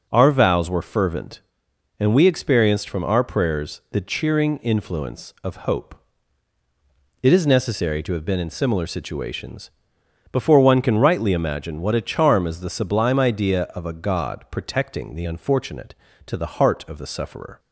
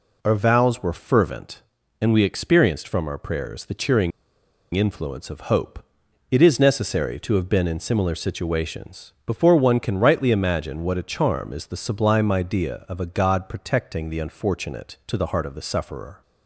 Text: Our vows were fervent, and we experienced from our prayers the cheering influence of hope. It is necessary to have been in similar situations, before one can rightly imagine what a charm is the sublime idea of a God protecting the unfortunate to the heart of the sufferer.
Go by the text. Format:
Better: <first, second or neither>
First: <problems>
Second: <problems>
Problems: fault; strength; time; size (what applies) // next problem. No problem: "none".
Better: first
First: none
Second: pauses between "cheering" and "influence"; noticeable; at 4.1 s; 0.63 s long